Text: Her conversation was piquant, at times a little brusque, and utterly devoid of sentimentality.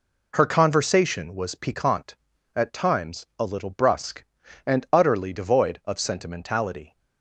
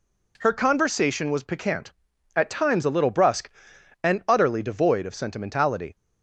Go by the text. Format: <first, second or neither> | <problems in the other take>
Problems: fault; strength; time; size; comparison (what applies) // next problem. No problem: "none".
neither | none